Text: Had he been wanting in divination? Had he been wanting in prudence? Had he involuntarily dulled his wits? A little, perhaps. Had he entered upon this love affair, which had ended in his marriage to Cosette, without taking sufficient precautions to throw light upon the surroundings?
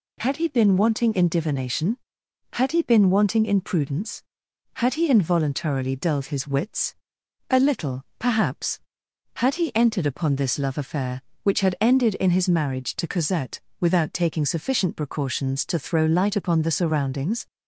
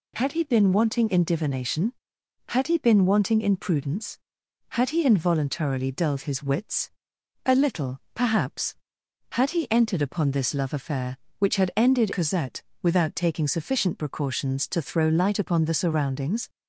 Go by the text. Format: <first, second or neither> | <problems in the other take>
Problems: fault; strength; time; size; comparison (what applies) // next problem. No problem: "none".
first | skips "in his marriage to"; at 12.1 s